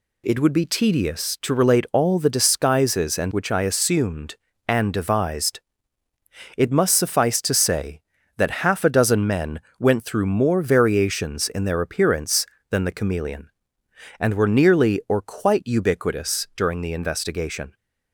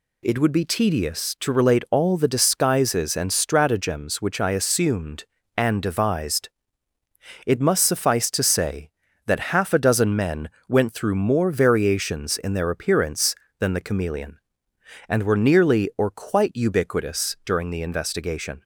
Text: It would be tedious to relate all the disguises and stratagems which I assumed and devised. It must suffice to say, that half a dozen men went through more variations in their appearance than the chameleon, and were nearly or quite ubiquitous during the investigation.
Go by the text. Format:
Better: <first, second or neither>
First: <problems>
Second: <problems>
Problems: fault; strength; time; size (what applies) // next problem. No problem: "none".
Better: second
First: skips "stratagems"; at 3.3 s // pauses between "men" and "went"; slight; at 9.5 s; 0.18 s long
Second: pauses between "men" and "went"; slight; at 10.4 s; 0.18 s long